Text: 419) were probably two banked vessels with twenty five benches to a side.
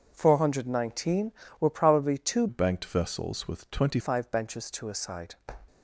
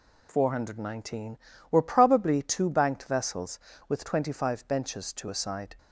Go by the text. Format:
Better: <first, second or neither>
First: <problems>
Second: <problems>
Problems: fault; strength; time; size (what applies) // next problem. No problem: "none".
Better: second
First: changes voice from "banked" to "twenty"; from 2.4 to 3.9 s; 1.5 s long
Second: none